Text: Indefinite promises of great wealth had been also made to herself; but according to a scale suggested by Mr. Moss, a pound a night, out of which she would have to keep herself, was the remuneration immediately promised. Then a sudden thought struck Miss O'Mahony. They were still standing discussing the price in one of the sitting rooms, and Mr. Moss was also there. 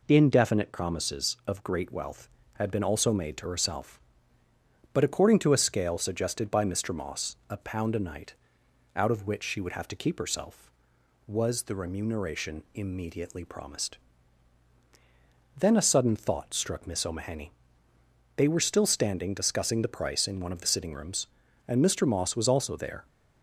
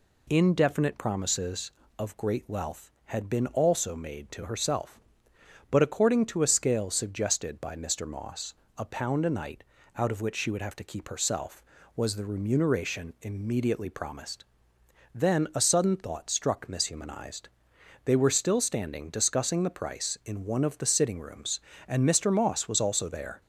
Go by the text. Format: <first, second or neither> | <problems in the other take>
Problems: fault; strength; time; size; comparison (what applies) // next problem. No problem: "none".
first | says "Humanized" for "O'Mahony"; at 16.8 s